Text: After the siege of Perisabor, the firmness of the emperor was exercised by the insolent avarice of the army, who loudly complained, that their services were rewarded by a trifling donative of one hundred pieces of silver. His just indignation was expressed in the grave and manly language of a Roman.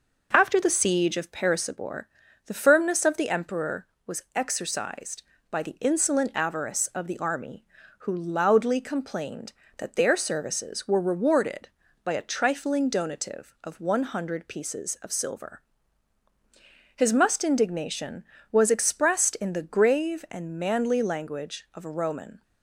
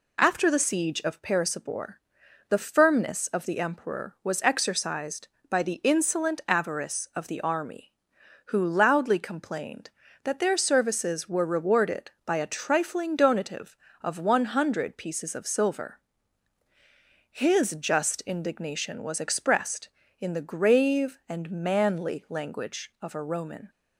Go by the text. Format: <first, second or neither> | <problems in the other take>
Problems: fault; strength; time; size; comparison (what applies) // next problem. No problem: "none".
second | says "must" for "just"; at 17.1 s